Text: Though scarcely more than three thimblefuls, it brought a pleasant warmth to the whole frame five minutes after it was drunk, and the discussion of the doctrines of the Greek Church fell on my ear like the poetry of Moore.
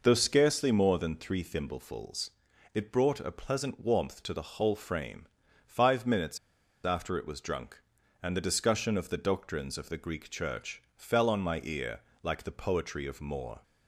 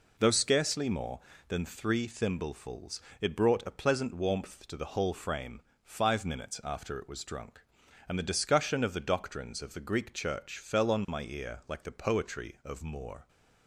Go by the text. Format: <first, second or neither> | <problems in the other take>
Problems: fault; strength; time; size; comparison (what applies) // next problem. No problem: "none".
second | pauses between "frame" and "five"; at 5.2 s; 0.40 s long; slight in the second // pauses between "minutes" and "after"; noticeable; at 6.3 s; 0.46 s long // pauses between "ear" and "like"; slight; at 12.0 s; 0.22 s long